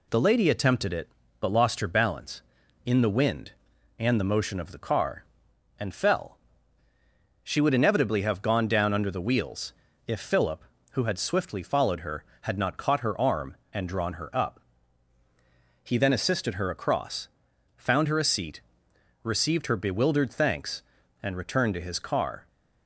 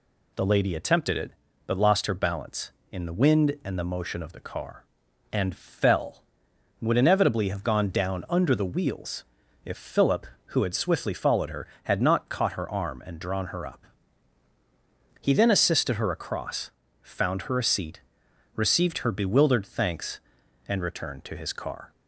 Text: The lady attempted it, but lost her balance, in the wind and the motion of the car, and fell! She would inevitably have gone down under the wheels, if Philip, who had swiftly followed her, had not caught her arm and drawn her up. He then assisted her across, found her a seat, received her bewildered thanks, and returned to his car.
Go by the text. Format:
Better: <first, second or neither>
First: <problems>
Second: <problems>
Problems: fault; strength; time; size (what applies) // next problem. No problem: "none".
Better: first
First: none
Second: skips "She"; at 6.5 s